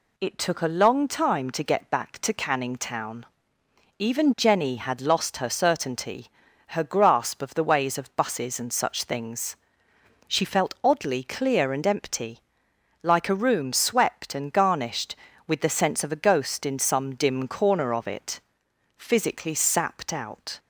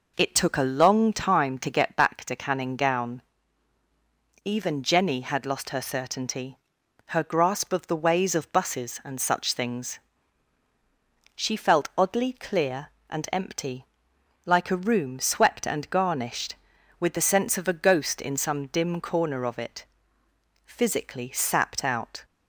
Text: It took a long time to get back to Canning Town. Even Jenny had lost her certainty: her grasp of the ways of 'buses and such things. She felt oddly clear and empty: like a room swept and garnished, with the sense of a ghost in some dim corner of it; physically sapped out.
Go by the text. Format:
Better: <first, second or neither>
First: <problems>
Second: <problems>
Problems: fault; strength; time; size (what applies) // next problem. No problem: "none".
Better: first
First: none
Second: says "Gown" for "Town"; at 2.7 s